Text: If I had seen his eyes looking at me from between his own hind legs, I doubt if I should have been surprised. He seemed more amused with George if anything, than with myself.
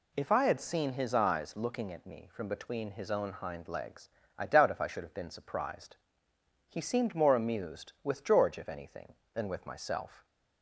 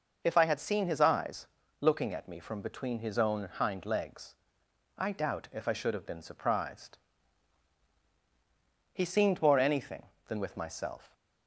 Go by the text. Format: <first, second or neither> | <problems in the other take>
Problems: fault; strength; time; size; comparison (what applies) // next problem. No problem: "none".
first | pauses between "eyes" and "looking"; slight; at 1.4 s; 0.32 s long // skips "amused with George if"; at 9.5 s